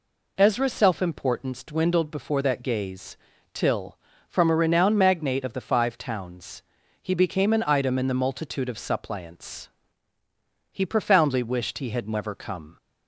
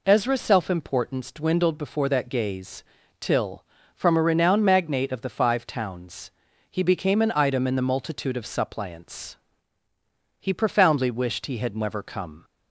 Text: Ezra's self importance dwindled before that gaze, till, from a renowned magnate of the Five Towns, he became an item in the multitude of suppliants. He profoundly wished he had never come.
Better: neither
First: none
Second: none

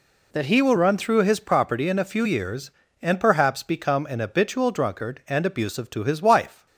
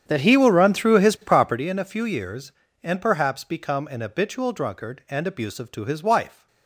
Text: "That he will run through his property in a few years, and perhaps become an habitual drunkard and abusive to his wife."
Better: first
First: none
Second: starts louder than the rest; strong; until 1.6 s; 8.5 dB

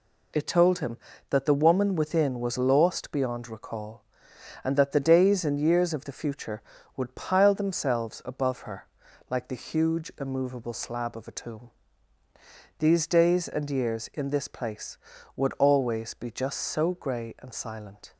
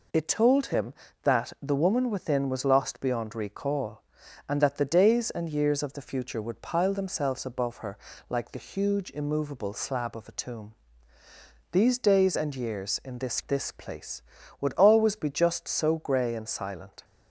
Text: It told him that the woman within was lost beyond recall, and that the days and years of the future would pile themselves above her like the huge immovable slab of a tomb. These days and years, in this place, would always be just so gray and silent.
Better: first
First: pauses between "her" and "like"; at 8.8 s; 0.42 s long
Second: pauses between "her" and "like"; slight; at 7.9 s; 0.32 s long // says "this" twice; at 13.4 s

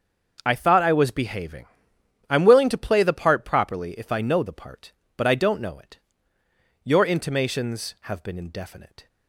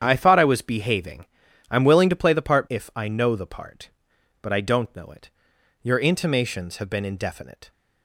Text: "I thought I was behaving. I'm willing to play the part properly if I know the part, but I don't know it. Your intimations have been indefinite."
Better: first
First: starts louder than the rest; until 1.4 s; 6 dB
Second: starts louder than the rest; strong; until 1.0 s; 9 dB // skips "properly"; at 2.6 s

